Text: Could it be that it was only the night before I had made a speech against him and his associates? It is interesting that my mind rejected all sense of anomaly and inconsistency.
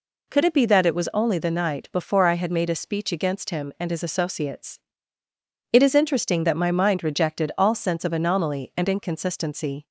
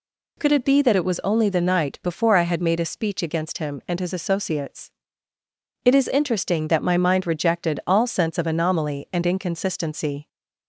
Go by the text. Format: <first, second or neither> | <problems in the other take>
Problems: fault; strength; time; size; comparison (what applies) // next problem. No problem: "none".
neither | none